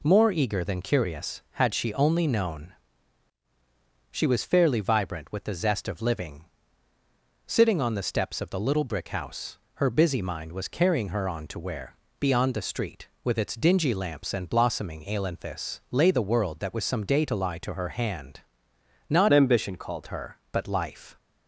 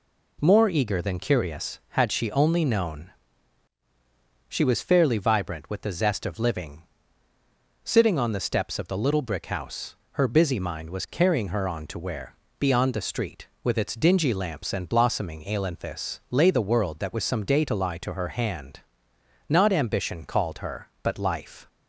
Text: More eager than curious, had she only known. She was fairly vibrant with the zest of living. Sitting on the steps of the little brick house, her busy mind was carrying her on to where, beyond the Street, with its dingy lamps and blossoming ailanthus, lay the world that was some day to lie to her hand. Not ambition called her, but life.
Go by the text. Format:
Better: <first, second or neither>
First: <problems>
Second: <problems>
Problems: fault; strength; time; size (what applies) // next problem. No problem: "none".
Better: second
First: changes voice from "ambition" to "called"; from 19.3 to 20.0 s; 0.7 s long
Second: none